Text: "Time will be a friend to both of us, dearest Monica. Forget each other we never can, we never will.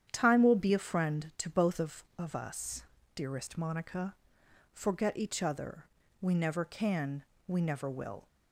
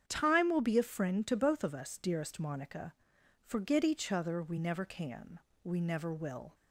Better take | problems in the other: second | starts louder than the rest; strong; until 1.1 s; 9 dB; strong in the second // says "of" twice; at 2.1 s // pauses between "other" and "we"; slight; at 5.8 s; 0.36 s long

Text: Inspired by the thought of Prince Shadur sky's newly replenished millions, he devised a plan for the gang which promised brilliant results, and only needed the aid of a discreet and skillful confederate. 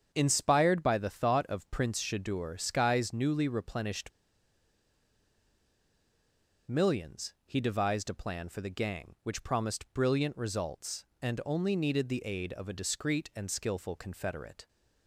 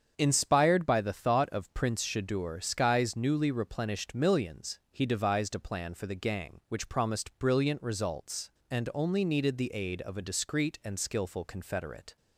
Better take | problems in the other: second | starts louder than the rest; strong; until 1.1 s; 7.5 dB; strong in the second // pauses between "replenished" and "millions"; strong; at 4.1 s; 2.5 s long

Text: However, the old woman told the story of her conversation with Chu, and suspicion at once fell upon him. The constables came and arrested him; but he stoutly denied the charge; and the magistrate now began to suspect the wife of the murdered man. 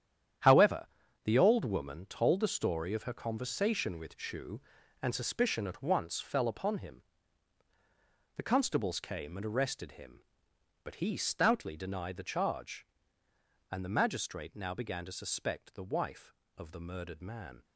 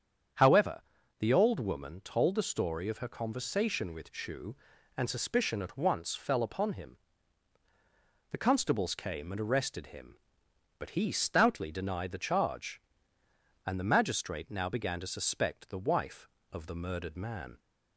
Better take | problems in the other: second | gets quieter; strong; throughout; 11 dB // starts louder than the rest; strong; until 1.8 s; 10 dB; strong in the second

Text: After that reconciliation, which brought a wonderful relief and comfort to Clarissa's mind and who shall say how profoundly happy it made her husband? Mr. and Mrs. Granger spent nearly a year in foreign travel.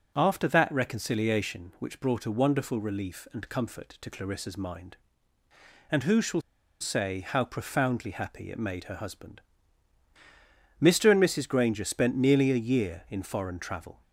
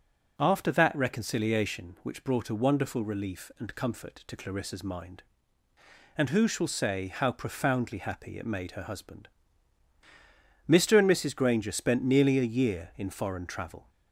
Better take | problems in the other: second | starts louder than the rest; noticeable; until 1.1 s; 6 dB; also in the second // pauses between "shall" and "say"; at 6.4 s; 0.39 s long

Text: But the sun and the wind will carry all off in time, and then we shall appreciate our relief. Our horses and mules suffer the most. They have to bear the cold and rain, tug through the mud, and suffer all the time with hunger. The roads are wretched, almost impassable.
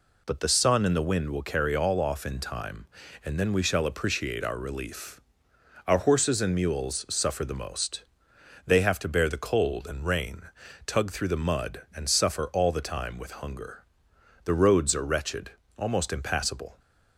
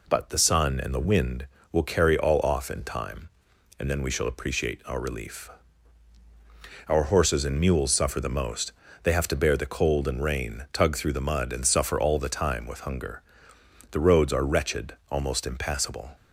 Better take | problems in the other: neither | none

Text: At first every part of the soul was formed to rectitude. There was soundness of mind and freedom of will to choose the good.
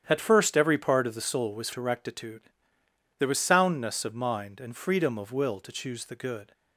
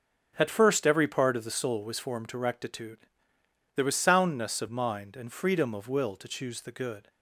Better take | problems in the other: second | starts louder than the rest; strong; until 1.0 s; 9.5 dB; strong in the second // skips "formed"; at 1.7 s

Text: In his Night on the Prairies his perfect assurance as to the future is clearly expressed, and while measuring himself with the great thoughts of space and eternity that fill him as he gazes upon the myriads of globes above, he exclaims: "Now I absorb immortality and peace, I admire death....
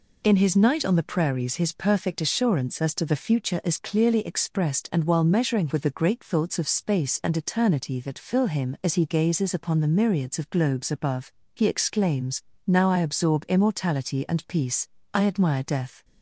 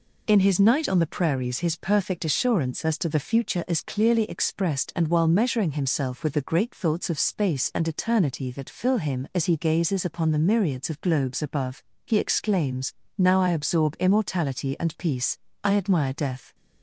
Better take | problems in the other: second | skips "himself"; at 5.7 s

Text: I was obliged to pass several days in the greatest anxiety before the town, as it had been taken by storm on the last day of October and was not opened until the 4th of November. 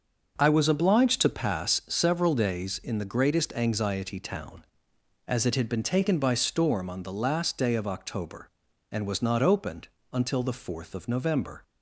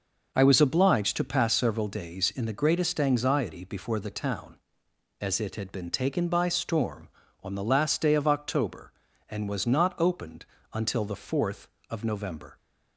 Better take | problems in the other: second | skips "before the"; at 4.1 s // pauses between "opened" and "until"; slight; at 9.8 s; 0.26 s long; slight in the second

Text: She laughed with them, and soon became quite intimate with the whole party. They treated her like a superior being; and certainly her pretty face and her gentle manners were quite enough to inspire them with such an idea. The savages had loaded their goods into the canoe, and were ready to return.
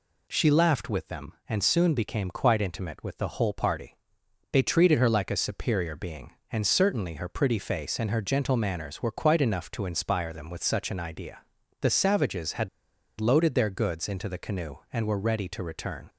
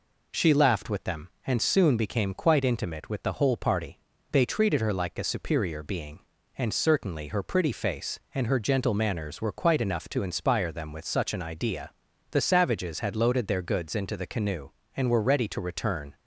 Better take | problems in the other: second | pauses between "had" and "loaded"; noticeable; at 12.6 s; 0.52 s long

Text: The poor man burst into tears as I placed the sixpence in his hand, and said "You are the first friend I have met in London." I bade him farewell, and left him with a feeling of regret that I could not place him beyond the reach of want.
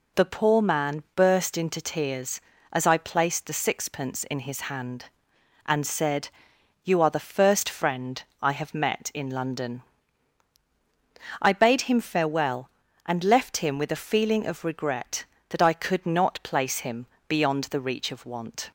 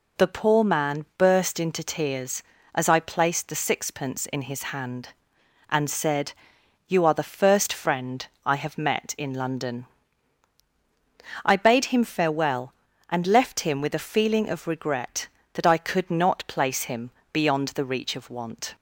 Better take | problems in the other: neither | pauses between "said" and "You"; noticeable; the same in both // pauses between "friend" and "I"; slight; the same in both // pauses between "him" and "beyond"; slight; the same in both

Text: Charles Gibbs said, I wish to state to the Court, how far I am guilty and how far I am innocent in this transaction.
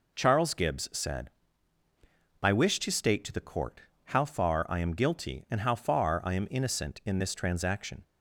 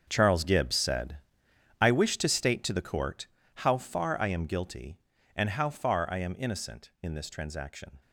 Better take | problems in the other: first | gets quieter; strong; throughout; 14.5 dB

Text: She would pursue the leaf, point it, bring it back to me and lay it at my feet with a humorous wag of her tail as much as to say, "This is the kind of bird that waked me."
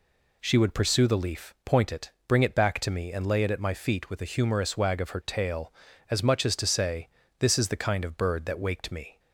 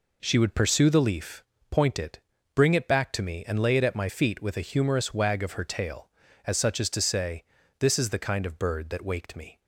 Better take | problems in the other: first | says "such" for "much"; at 6.5 s

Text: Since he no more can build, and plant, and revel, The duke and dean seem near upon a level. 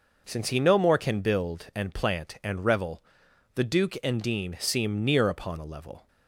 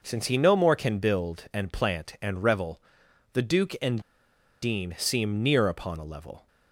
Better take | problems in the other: first | pauses between "and" and "dean"; noticeable; at 4.0 s; 0.61 s long

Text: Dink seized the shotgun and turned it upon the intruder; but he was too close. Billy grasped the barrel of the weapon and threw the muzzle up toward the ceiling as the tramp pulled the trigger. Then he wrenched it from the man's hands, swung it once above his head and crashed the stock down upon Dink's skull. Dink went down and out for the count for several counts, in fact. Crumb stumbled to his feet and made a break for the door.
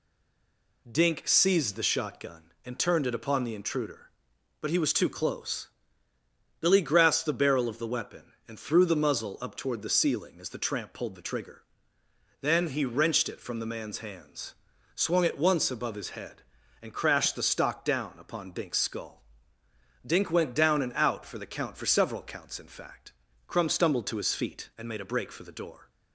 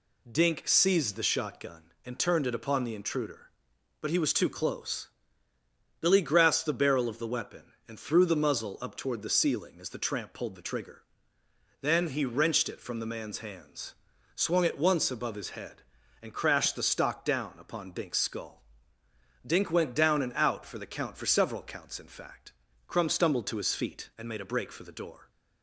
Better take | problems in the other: second | stays silent before the first word; slight; until 0.8 s; 0.8 s long

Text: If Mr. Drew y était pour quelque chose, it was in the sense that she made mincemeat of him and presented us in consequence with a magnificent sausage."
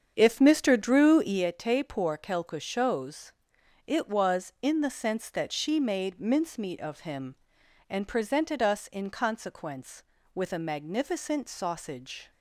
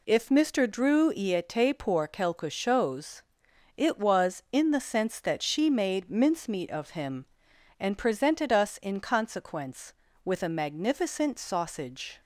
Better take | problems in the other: second | starts louder than the rest; strong; until 1.5 s; 7.5 dB

